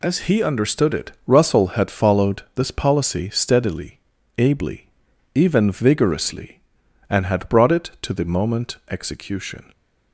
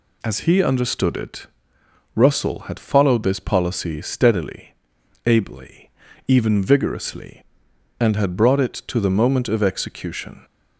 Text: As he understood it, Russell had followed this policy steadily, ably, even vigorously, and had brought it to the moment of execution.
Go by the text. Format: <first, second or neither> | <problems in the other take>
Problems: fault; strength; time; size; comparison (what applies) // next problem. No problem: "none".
second | skips "of"; at 8.8 s